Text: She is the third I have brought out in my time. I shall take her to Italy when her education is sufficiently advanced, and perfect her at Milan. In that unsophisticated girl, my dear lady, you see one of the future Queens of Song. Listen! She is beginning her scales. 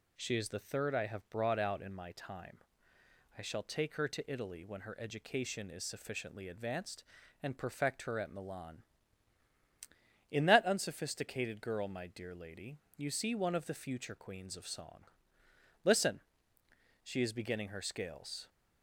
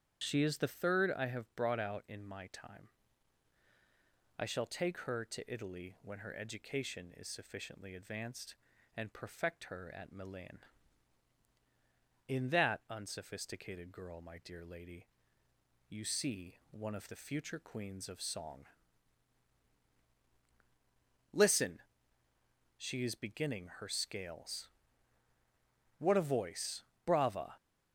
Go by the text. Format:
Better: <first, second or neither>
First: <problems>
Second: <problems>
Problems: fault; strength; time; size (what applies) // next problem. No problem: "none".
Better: first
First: none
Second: starts louder than the rest; strong; until 1.2 s; 8.5 dB // goes on to say "What a voice Brava"; from 25.9 s on; 1.5 s long